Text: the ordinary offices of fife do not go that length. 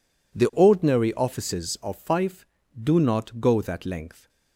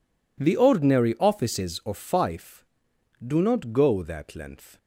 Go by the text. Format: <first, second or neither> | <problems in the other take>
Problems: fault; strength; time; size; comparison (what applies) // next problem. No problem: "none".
neither | none